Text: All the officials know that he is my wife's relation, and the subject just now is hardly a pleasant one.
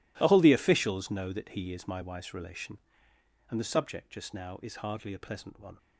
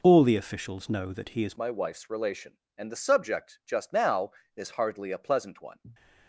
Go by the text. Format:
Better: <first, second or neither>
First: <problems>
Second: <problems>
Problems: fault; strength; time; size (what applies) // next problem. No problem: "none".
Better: first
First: none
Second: changes voice at "my"; from 1.5 s on; 4.2 s long